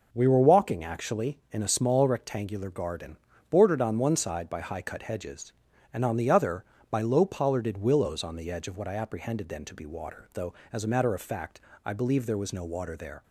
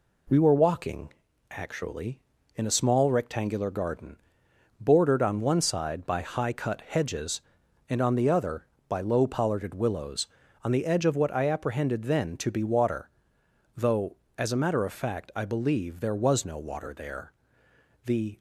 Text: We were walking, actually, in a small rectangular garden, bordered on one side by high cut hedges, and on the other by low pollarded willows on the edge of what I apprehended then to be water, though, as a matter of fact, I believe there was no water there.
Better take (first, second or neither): first